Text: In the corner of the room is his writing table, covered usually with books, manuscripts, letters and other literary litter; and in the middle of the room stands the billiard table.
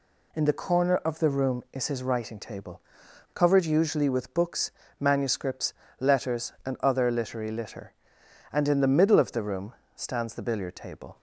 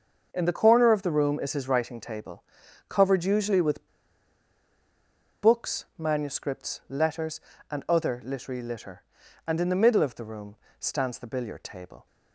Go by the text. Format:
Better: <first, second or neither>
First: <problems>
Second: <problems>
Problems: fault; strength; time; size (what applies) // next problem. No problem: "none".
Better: first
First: pauses between "room" and "stands"; slight; at 9.7 s; 0.20 s long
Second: starts louder than the rest; until 1.3 s; 6.5 dB // pauses between "with" and "books"; strong; at 3.8 s; 1.5 s long // pauses between "room" and "stands"; slight; at 10.5 s; 0.24 s long